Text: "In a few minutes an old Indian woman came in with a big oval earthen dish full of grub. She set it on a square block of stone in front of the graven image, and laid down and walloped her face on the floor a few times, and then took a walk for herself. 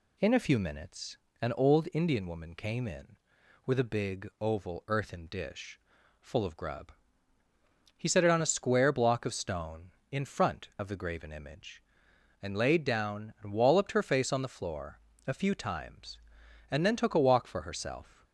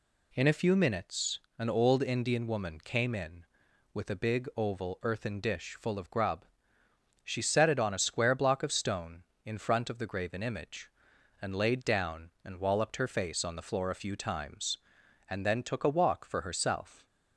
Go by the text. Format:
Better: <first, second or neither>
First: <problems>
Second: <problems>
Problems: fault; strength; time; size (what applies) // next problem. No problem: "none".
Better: second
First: pauses between "minutes" and "an"; slight; at 1.1 s; 0.26 s long // pauses between "dish" and "full"; at 5.7 s; 0.40 s long // says "He" for "She"; at 7.9 s // pauses between "floor" and "a"; slight; at 14.9 s; 0.26 s long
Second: pauses between "minutes" and "an"; slight; at 1.4 s; 0.18 s long